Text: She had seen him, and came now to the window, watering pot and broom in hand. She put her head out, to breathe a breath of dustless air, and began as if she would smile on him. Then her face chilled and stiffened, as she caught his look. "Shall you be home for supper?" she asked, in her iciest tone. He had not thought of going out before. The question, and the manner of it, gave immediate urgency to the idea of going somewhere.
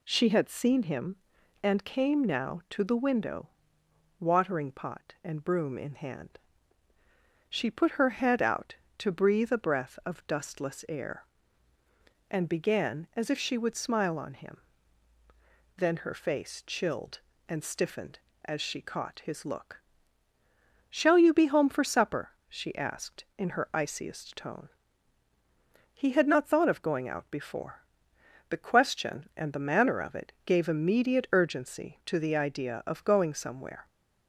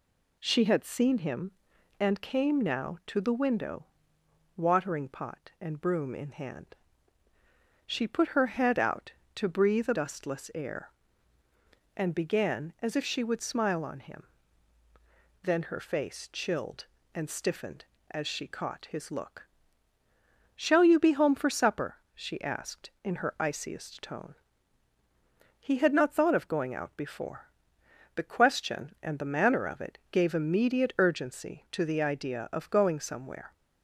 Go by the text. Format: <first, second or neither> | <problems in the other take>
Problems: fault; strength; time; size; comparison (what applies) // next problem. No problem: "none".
first | skips "breath of"; at 9.9 s